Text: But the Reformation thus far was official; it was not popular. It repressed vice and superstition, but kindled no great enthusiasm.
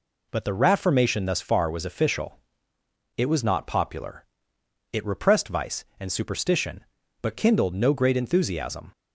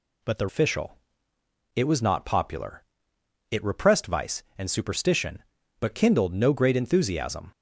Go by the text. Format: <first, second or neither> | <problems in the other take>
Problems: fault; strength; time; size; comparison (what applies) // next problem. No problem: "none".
first | skips "Reformation thus far was"; at 0.4 s